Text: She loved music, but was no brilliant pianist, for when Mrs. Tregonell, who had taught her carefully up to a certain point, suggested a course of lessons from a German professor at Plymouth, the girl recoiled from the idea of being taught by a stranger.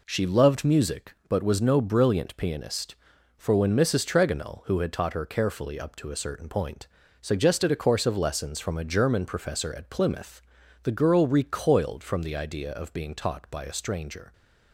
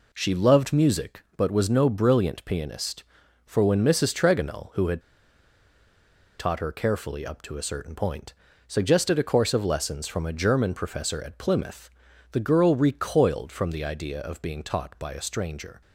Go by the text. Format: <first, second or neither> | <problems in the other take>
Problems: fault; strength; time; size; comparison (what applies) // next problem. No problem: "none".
first | pauses between "had" and "taught"; strong; at 5.0 s; 1.3 s long